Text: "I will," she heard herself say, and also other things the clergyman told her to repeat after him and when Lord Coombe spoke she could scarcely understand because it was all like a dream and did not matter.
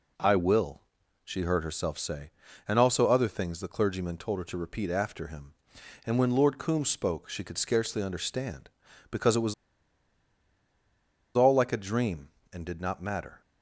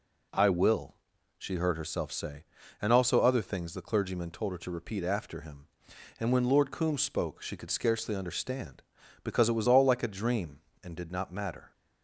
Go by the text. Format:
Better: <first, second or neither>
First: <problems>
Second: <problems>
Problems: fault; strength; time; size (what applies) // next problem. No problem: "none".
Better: second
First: pauses between "was" and "all"; strong; at 9.5 s; 1.8 s long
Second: none